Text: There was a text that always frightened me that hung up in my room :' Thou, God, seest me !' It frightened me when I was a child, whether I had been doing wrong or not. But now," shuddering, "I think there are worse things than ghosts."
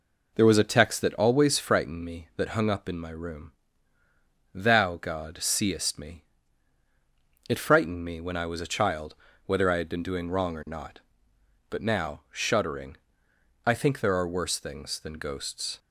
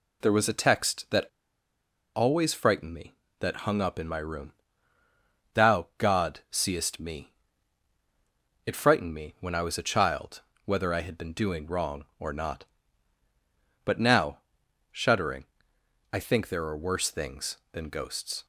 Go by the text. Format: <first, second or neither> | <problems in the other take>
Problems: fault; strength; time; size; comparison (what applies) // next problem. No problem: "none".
first | pauses between "that" and "always"; noticeable; at 1.2 s; 0.88 s long